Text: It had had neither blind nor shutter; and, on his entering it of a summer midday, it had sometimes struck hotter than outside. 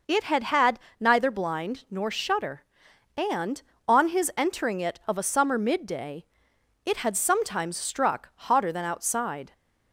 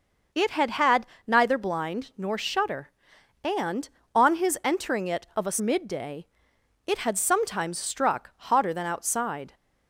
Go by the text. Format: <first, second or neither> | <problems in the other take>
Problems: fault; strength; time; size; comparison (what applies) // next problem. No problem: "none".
first | pauses between "had" and "neither"; slight; at 1.0 s; 0.20 s long; slight in the first // skips "summer"; at 5.5 s